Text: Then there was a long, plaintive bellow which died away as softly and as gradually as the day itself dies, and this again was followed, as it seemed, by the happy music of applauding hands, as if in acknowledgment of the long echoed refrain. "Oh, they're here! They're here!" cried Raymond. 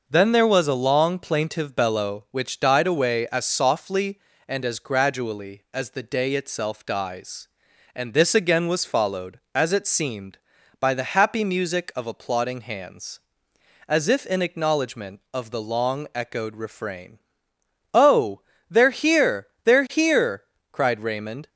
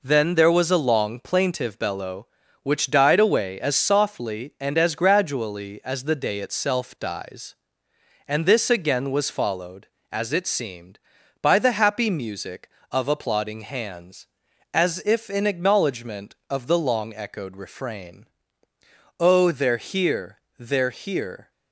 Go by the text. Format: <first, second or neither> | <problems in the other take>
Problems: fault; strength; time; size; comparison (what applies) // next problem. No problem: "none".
first | stops before "cried Raymond"; at 21.5 s